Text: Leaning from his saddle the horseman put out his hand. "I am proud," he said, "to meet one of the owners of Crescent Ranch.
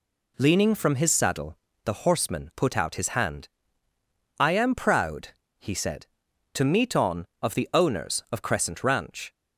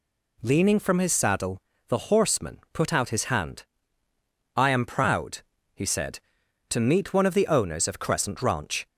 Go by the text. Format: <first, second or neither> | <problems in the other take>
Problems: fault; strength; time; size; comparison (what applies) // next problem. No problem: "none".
second | pauses between "saddle" and "the"; slight; at 1.5 s; 0.28 s long; slight in the second // says "on" for "one"; at 6.9 s